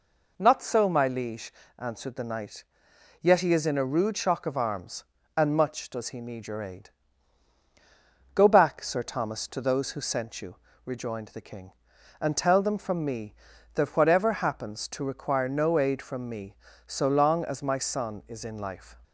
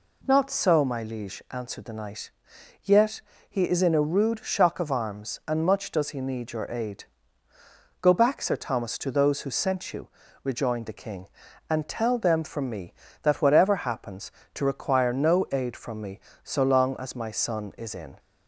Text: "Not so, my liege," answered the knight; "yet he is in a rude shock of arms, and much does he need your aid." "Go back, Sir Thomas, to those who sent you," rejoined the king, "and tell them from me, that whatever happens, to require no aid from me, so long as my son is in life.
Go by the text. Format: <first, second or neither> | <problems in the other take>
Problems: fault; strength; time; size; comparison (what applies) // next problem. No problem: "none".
first | pauses between "yet" and "he"; slight; at 3.2 s; 0.30 s long // stops before "life"; at 18.1 s